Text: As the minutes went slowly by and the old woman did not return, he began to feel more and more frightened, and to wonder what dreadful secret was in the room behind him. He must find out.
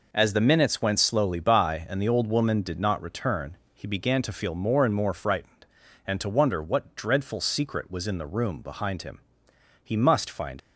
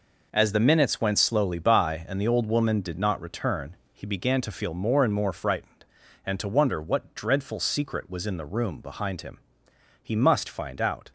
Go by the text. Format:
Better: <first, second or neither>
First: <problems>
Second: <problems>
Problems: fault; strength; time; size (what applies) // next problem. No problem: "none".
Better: second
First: stops before "out"; at 10.5 s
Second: none